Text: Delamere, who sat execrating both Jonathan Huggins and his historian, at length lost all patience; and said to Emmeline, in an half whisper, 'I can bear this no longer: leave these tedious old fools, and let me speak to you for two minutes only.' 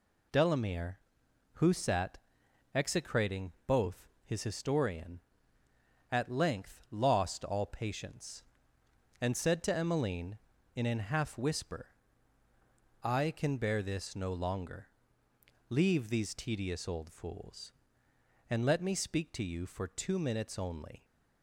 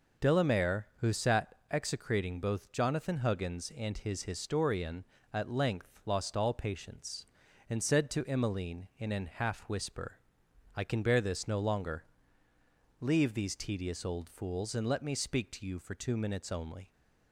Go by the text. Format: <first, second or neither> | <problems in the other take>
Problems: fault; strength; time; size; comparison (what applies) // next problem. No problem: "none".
second | pauses between "sat" and "execrating"; noticeable; at 2.1 s; 0.58 s long; slight in the second // skips "Jonathan Huggins and"; at 4.1 s